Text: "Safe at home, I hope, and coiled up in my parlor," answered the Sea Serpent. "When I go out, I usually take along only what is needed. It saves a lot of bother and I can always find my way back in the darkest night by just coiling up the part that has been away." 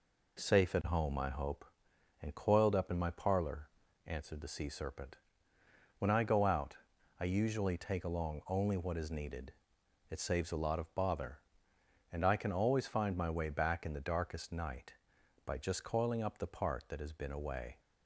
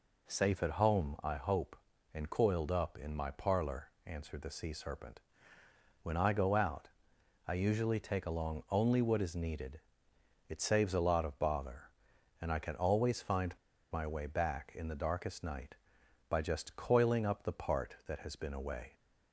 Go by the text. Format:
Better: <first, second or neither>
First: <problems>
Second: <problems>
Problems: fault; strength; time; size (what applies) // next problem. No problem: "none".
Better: first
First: none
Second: pauses between "find" and "my"; at 13.5 s; 0.36 s long